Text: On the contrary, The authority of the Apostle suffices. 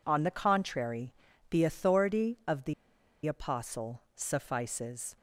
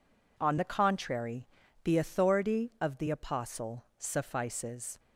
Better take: second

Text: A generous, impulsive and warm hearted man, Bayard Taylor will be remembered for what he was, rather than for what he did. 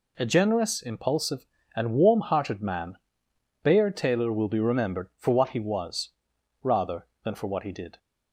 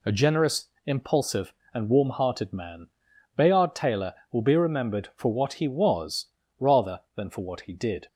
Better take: neither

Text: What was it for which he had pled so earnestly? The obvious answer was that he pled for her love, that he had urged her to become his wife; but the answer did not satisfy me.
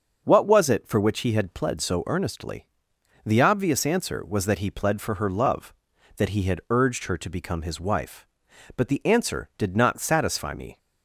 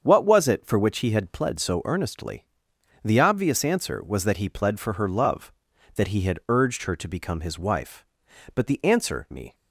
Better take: first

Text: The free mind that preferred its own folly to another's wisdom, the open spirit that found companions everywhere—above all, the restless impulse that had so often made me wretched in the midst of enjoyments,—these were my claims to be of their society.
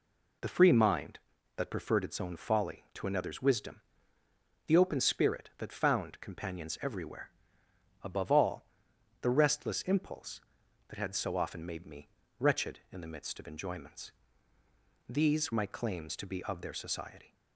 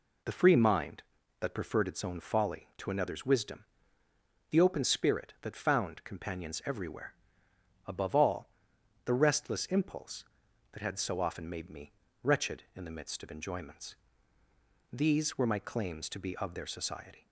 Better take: second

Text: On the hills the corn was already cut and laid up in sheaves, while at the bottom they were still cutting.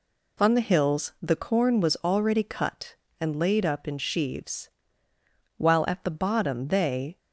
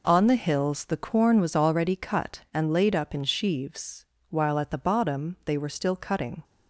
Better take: second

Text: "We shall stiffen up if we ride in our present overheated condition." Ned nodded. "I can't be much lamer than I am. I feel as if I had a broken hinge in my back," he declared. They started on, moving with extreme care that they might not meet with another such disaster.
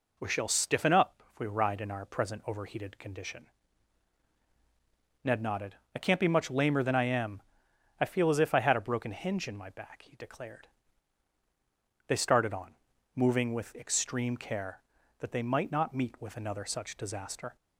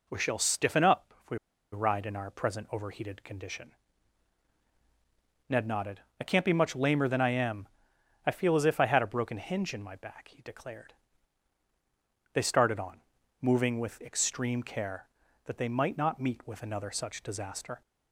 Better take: first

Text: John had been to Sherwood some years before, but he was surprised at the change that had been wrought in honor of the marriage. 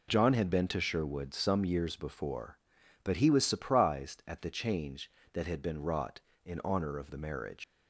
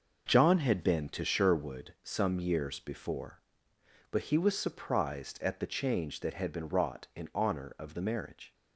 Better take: second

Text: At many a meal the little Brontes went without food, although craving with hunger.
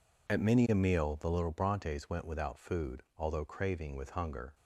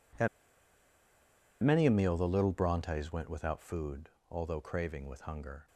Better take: first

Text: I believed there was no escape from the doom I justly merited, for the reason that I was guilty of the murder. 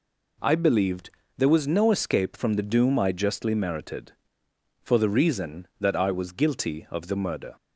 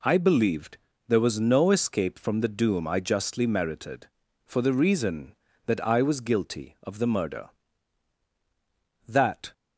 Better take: first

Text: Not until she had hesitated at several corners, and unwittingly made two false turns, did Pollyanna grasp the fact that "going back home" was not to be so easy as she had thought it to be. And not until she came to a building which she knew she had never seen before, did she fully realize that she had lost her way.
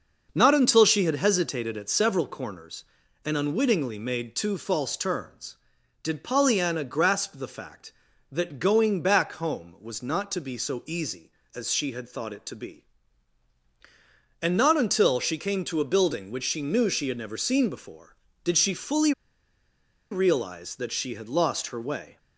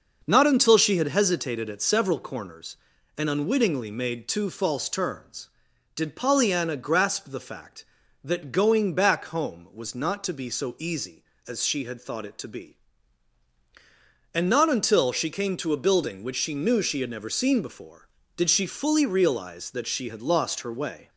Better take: second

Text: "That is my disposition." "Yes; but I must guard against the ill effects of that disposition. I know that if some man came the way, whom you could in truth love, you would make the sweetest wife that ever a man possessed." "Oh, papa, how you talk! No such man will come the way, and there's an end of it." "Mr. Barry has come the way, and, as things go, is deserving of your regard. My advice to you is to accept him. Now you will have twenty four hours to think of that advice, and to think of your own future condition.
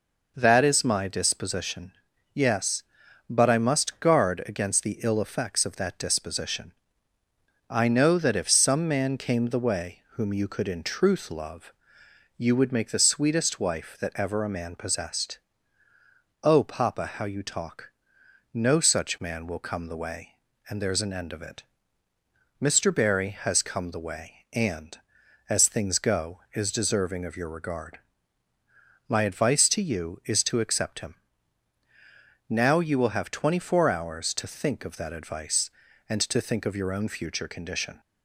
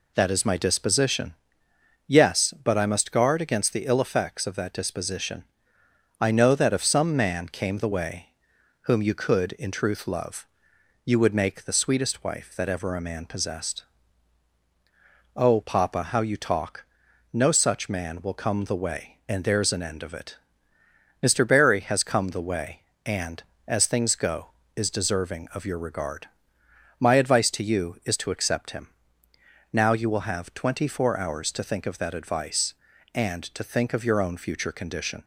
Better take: neither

